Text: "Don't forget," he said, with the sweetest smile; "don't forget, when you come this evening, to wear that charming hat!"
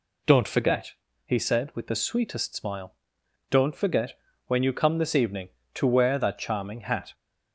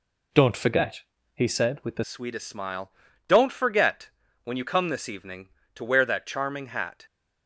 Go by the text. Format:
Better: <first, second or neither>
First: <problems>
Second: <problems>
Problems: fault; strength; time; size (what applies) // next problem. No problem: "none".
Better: first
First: none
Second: changes voice at "sweetest"; from 2.0 s on; 5.0 s long